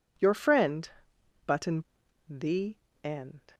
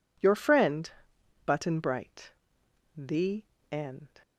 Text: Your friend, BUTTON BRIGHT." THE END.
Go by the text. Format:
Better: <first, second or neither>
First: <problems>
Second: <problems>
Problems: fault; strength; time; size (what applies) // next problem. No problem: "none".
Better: second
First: skips "BRIGHT"; at 2.0 s // pauses between "THE" and "END"; slight; at 2.7 s; 0.26 s long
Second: pauses between "THE" and "END"; slight; at 3.4 s; 0.26 s long